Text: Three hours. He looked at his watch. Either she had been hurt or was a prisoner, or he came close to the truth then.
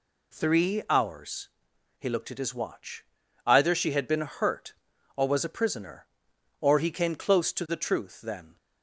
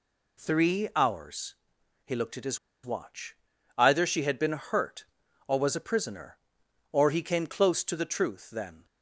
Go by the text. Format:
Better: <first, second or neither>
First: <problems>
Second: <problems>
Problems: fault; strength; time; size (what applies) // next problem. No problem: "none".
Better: first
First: none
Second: pauses between "his" and "watch"; slight; at 2.5 s; 0.27 s long